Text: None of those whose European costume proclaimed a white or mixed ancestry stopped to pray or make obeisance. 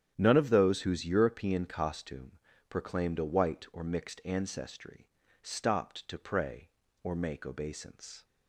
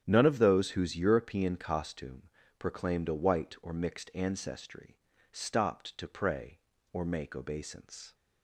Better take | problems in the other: neither | starts louder than the rest; strong; the same in both // pauses between "costume" and "proclaimed"; slight; the same in both // pauses between "ancestry" and "stopped"; slight; the same in both

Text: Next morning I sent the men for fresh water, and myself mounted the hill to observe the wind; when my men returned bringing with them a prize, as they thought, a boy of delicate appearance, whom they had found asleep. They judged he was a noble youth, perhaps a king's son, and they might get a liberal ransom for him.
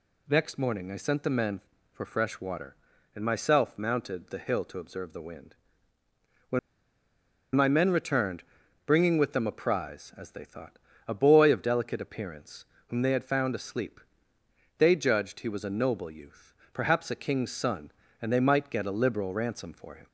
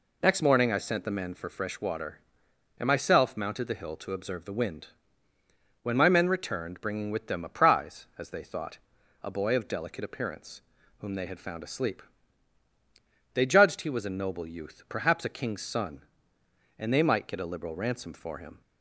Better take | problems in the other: second | pauses between "when" and "my"; noticeable; at 6.5 s; 0.95 s long // pauses between "returned" and "bringing"; noticeable; at 8.4 s; 0.46 s long

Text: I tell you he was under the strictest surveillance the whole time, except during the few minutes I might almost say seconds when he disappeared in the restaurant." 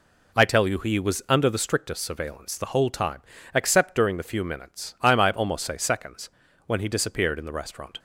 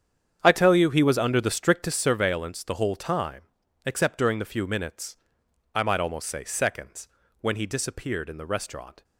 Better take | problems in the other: first | starts louder than the rest; strong; until 2.2 s; 8.5 dB // pauses between "minutes" and "I"; noticeable; at 5.1 s; 0.58 s long // pauses between "seconds" and "when"; slight; at 7.0 s; 0.34 s long; slight in the first

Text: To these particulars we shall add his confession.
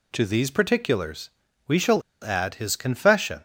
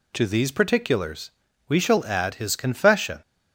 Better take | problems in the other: second | pauses between "particulars" and "we"; at 1.2 s; 0.38 s long; also in the second // pauses between "shall" and "add"; slight; at 2.0 s; 0.21 s long

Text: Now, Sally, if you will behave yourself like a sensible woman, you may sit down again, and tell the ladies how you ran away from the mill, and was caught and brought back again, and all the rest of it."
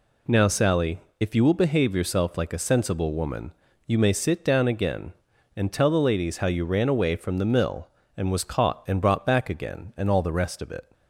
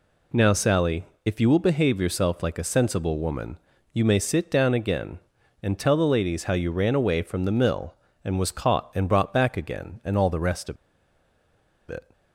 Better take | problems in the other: first | pauses between "of" and "it"; at 10.7 s; 1.1 s long

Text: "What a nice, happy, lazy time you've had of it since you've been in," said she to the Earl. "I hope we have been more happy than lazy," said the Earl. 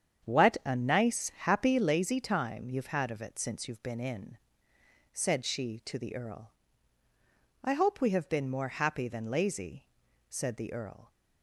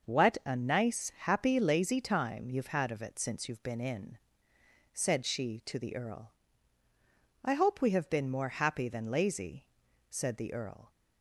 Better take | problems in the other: second | starts louder than the rest; strong; until 1.8 s; 8 dB

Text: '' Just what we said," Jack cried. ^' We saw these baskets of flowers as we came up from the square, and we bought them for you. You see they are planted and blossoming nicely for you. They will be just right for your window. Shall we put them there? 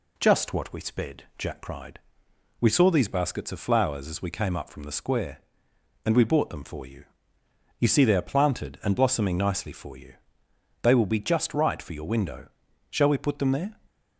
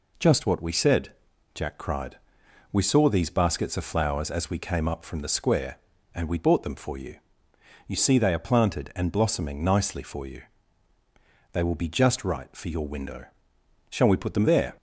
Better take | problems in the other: second | says "sped" for "said"; at 0.8 s

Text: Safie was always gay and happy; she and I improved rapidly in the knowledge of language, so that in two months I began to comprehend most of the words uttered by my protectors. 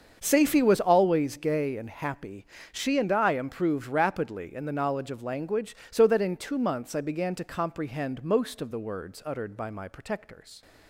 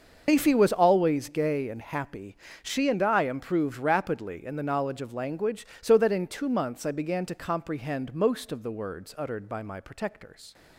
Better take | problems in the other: first | loses the start of "Safie"; at 0.2 s; 150 ms // starts louder than the rest; until 1.3 s; 6 dB; also in the first

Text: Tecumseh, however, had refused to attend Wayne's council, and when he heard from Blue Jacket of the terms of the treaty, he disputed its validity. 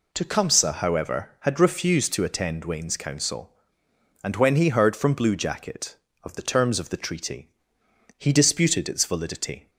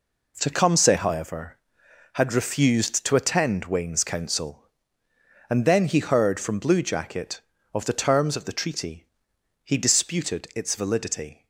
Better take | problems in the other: first | says "then" for "when"; at 5.6 s

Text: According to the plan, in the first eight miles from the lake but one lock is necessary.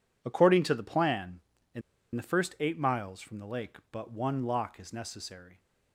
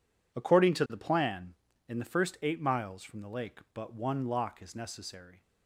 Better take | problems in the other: second | pauses between "in" and "the"; slight; at 1.8 s; 0.34 s long

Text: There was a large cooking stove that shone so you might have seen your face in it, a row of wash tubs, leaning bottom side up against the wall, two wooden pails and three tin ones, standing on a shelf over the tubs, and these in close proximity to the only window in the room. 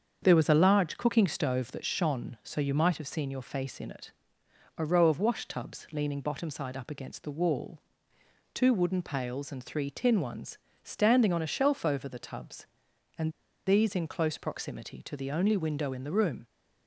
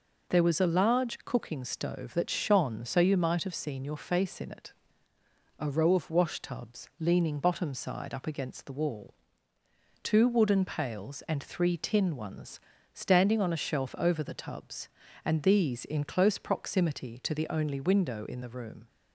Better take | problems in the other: second | starts louder than the rest; strong; until 1.2 s; 7 dB // pauses between "and" and "these"; slight; at 13.3 s; 0.35 s long

